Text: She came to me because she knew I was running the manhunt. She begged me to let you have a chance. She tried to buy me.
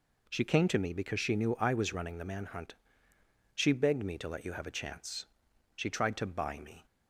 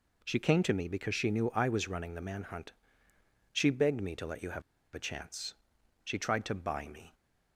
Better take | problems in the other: first | pauses between "have" and "a"; slight; at 4.6 s; 0.33 s long

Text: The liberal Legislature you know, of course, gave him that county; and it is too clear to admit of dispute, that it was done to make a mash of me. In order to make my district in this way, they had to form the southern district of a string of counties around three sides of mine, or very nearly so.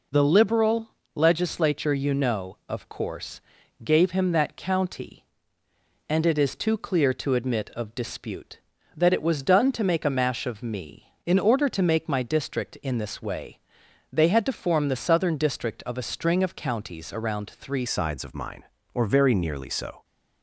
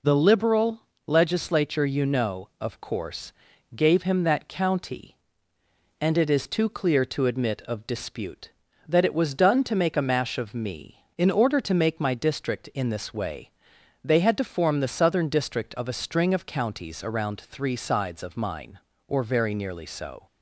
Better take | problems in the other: second | pauses between "liberal" and "Legislature"; slight; at 0.8 s; 0.28 s long; slight in the second // changes voice at "sides"; from 17.8 s on; 2.2 s long

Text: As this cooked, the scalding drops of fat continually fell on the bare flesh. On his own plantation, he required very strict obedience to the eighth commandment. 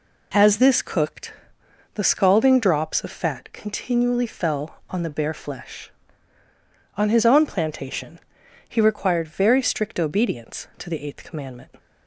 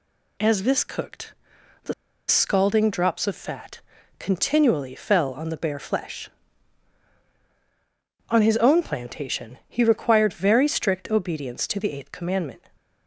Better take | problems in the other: first | pauses between "the" and "scalding"; slight; at 1.9 s; 0.34 s long // pauses between "fat" and "continually"; at 3.8 s; 0.40 s long

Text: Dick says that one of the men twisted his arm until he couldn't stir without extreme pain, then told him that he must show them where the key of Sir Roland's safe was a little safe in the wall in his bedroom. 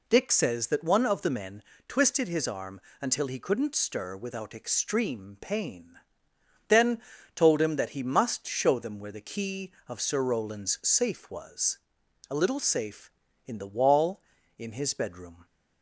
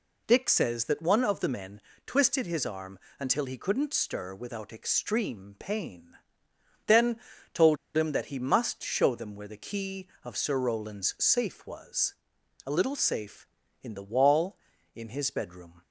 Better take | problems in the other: first | pauses between "men" and "twisted"; slight; at 1.7 s; 0.26 s long; slight in the first // pauses between "arm" and "until"; slight; at 2.9 s; 0.22 s long; slight in the first // pauses between "then" and "told"; slight; at 7.1 s; 0.34 s long; slight in the first // pauses between "told" and "him"; slight; at 7.7 s; 0.18 s long // pauses between "was" and "a"; noticeable; at 12.1 s; 0.52 s long; noticeable in the first

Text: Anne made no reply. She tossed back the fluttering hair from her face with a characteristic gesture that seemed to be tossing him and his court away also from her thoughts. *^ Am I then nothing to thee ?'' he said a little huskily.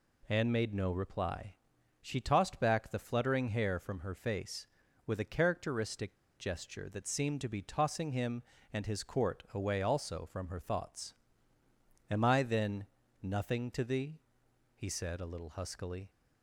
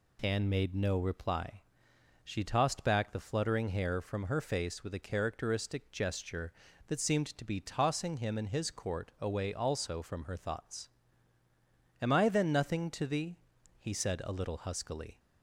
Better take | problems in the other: second | pauses between "characteristic" and "gesture"; slight; at 6.1 s; 0.20 s long // pauses between "then" and "nothing"; slight; at 12.8 s; 0.36 s long

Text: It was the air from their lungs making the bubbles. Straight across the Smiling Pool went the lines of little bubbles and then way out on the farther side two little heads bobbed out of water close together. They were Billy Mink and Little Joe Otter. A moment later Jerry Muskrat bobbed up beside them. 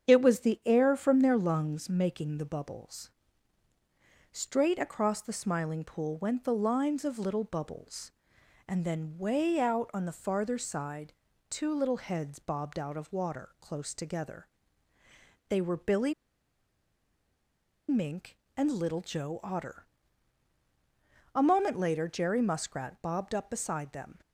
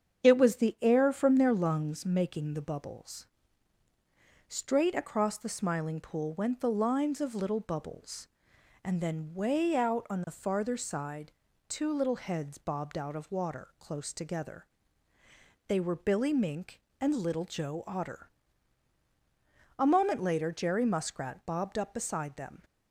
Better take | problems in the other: second | starts louder than the rest; strong; until 1.1 s; 8 dB; strong in the second // pauses between "side" and "two"; slight; at 11.1 s; 0.36 s long; slight in the second // pauses between "Billy" and "Mink"; strong; at 16.1 s; 1.7 s long

